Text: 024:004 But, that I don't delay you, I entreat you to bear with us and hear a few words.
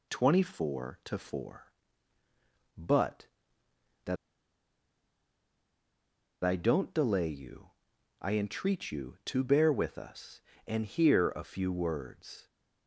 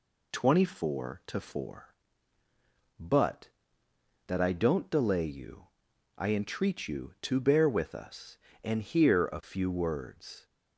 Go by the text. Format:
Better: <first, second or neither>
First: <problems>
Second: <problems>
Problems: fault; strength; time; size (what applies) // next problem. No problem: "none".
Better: second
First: pauses between "that" and "I"; strong; at 4.1 s; 2.2 s long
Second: none